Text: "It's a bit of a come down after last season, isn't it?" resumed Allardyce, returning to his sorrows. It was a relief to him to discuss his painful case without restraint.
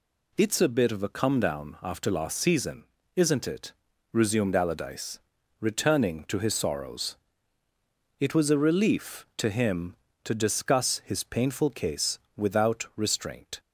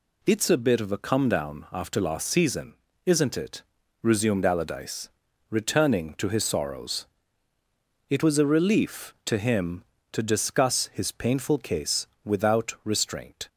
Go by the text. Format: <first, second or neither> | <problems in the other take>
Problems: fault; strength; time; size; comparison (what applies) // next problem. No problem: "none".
neither | pauses between "case" and "without"; slight; the same in both